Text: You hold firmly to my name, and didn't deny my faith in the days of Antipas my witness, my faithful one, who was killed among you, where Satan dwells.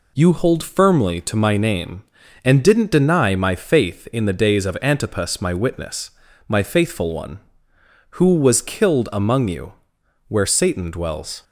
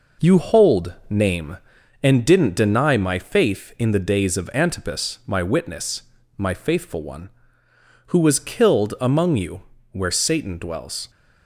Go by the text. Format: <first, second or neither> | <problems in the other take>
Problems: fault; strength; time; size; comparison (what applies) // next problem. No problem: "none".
first | skips "firmly to my"; at 1.0 s